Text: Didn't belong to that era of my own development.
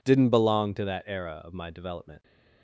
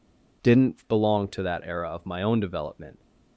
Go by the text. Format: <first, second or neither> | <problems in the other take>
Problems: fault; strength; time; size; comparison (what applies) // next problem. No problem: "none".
second | skips "own"; at 1.6 s